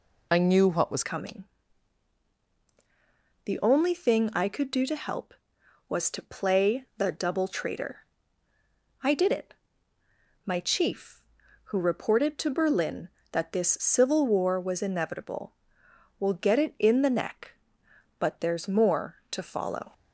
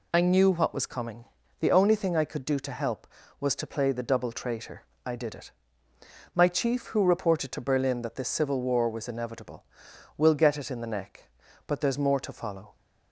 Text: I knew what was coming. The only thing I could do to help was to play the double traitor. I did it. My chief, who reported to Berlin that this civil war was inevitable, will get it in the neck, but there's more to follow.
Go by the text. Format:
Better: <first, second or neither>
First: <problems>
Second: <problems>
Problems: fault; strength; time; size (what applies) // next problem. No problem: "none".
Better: second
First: changes voice at "coming"; from 1.0 s on; 18.9 s long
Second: none